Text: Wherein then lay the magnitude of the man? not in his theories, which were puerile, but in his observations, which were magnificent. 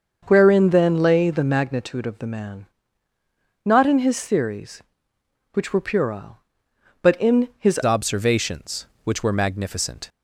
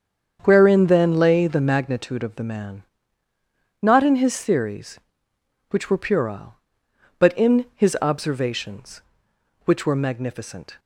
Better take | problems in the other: second | starts louder than the rest; until 1.2 s; 6 dB; strong in the second // changes voice at "observations"; from 7.8 s on; 2.2 s long

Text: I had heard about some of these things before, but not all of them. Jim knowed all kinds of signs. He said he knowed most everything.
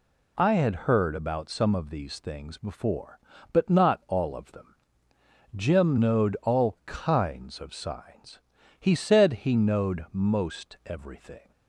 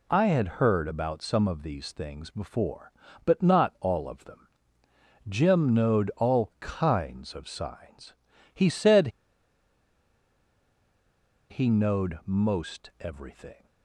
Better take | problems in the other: first | pauses between "said" and "he"; strong; at 9.0 s; 2.4 s long

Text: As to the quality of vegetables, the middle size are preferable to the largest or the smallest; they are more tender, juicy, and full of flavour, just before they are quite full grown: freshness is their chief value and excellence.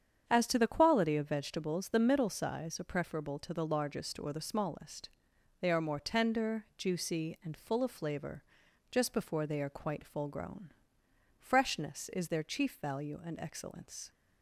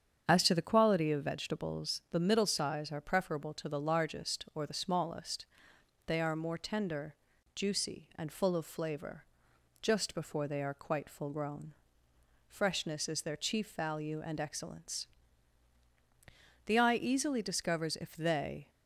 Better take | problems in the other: first | starts louder than the rest; strong; until 1.3 s; 8 dB; strong in the first // goes on to say "The eye easily discovers if they"; strong; from 16.6 s on; 2.0 s long

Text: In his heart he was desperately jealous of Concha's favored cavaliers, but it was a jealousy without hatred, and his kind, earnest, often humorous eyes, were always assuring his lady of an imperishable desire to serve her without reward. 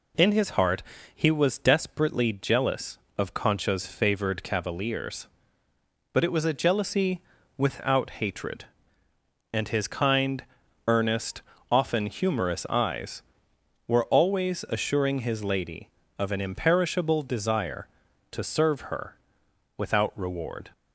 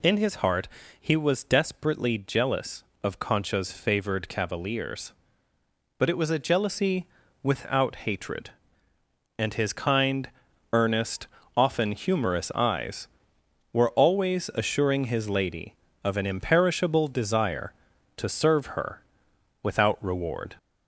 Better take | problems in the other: first | gets louder; slight; throughout; 3 dB // pauses between "heart" and "he"; slight; at 0.6 s; 0.32 s long; slight in the first // pauses between "jealousy" and "without"; at 7.0 s; 0.38 s long; also in the first // pauses between "her" and "without"; noticeable; at 19.0 s; 0.58 s long; noticeable in the first

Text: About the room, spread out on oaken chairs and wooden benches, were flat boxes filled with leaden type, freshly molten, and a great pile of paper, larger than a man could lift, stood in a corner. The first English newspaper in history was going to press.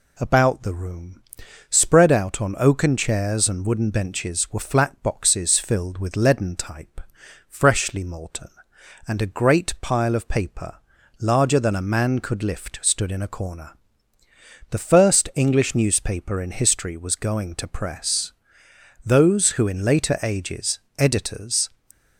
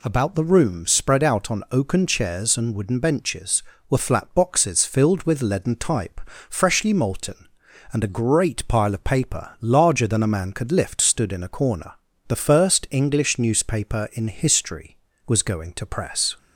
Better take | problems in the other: second | goes on to say "Those who in later ages editors"; strong; from 19.0 s on; 2.6 s long

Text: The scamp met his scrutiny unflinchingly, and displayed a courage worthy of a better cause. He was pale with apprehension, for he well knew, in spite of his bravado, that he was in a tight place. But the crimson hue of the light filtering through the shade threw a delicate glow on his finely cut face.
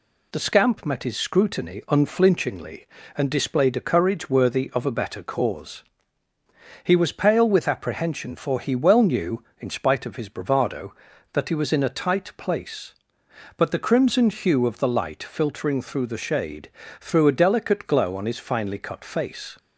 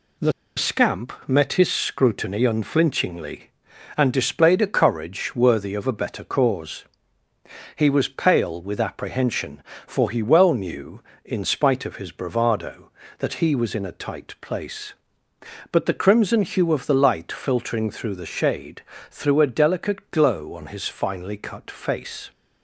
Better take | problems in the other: first | pauses between "The" and "scamp"; slight; at 0.3 s; 0.24 s long // pauses between "shade" and "threw"; slight; at 18.8 s; 0.30 s long; slight in the first

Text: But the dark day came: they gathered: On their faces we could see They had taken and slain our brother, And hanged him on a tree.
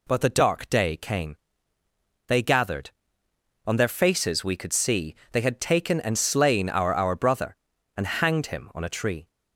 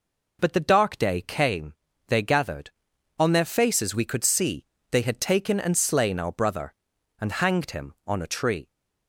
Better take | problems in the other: second | pauses between "see" and "They"; slight; at 5.1 s; 0.20 s long; slight in the second // says "our" twice; at 6.9 s

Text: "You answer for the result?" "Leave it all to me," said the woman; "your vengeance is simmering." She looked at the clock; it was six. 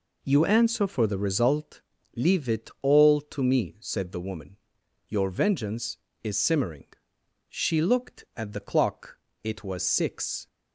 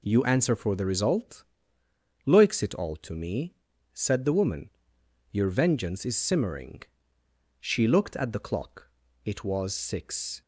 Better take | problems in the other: first | says "Loiks" for "Leave"; at 2.2 s

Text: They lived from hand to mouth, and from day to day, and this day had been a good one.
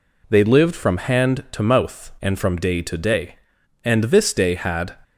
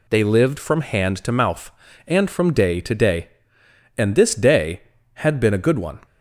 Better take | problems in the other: second | stops before "been a good one"; at 5.0 s

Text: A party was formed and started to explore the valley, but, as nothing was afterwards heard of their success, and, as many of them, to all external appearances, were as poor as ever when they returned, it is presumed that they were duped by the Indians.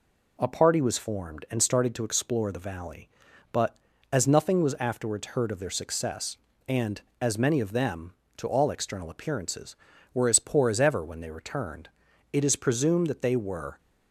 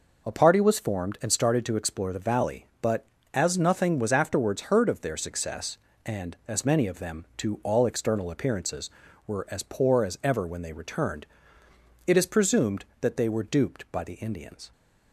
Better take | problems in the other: second | stops before "duped by the Indians"; at 13.7 s

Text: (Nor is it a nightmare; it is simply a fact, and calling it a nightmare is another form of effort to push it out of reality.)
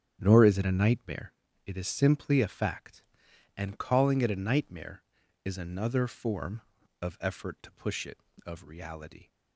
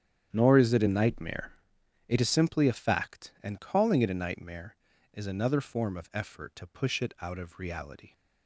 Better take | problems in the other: second | starts louder than the rest; strong; until 1.2 s; 8.5 dB; strong in the second // skips "out"; at 8.3 s

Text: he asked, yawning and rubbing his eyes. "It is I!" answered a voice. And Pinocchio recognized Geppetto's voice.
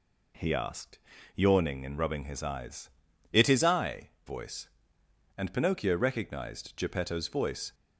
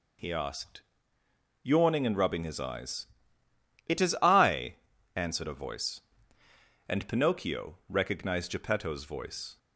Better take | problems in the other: second | skips "answered a"; at 4.1 s

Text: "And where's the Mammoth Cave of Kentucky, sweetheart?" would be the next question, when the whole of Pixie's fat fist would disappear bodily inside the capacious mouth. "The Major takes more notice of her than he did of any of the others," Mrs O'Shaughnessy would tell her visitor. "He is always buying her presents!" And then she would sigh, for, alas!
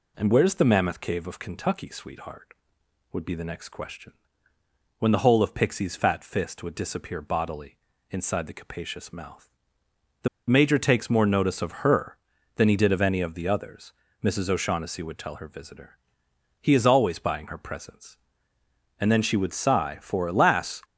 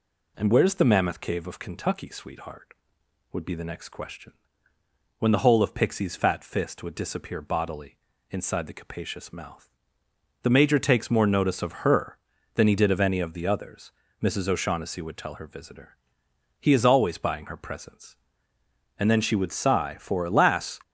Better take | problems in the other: second | pauses between "bodily" and "inside"; slight; at 7.7 s; 0.32 s long; slight in the second // pauses between "The" and "Major"; slight; at 10.2 s; 0.20 s long

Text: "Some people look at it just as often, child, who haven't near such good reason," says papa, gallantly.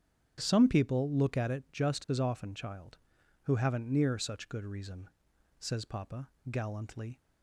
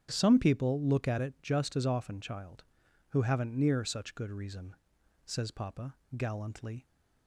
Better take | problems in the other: neither | starts louder than the rest; strong; the same in both

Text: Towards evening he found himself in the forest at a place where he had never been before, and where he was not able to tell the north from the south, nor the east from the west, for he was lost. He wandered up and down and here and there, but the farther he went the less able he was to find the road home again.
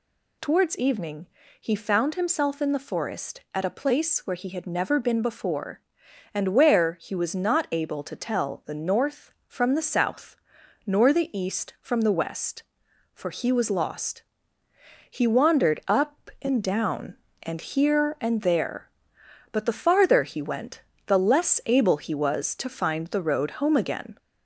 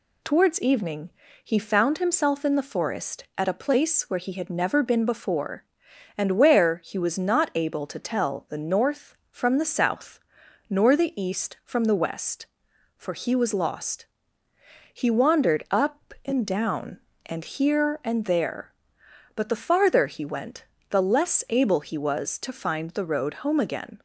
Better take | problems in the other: second | gets louder; slight; throughout; 2.5 dB // pauses between "evening" and "he"; slight; at 1.2 s; 0.34 s long; slight in the second // pauses between "went" and "the"; slight; at 20.8 s; 0.26 s long; slight in the second

